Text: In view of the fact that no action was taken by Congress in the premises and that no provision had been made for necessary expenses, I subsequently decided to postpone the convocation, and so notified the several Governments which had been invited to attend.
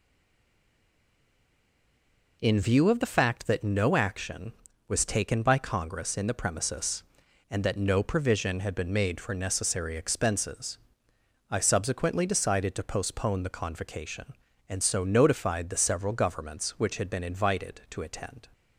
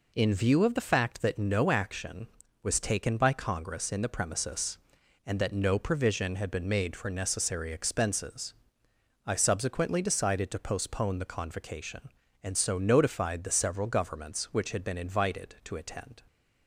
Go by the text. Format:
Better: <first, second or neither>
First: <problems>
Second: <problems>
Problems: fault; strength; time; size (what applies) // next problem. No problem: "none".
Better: second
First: stays silent before the first word; until 2.4 s; 2.4 s long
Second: none